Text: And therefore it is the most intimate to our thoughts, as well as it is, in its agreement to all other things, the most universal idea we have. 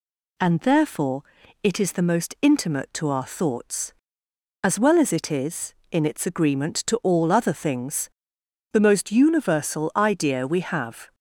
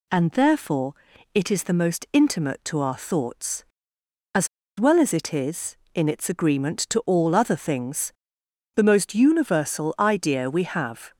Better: first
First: pauses between "therefore" and "it"; at 1.2 s; 0.40 s long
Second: pauses between "therefore" and "it"; at 0.9 s; 0.40 s long // pauses between "as" and "well"; slight; at 4.4 s; 0.31 s long

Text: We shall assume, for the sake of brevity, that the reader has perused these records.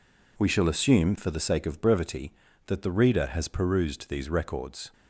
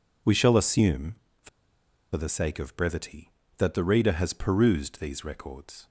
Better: first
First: none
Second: pauses between "for" and "the"; noticeable; at 1.4 s; 0.66 s long

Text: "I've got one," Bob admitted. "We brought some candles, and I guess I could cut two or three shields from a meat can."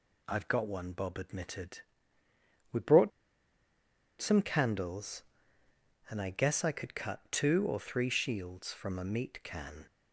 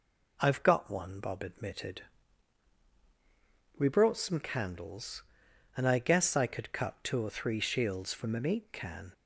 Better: second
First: pauses between "brought" and "some"; at 3.1 s; 1.1 s long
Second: none

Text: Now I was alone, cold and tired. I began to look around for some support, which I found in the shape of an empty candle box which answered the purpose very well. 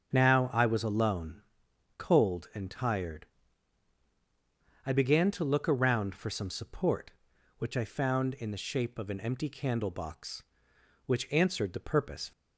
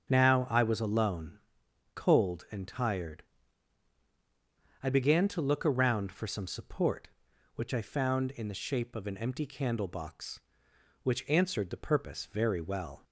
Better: second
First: starts louder than the rest; until 1.1 s; 7 dB // stops before "very well"; at 12.3 s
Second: starts louder than the rest; until 1.1 s; 7 dB

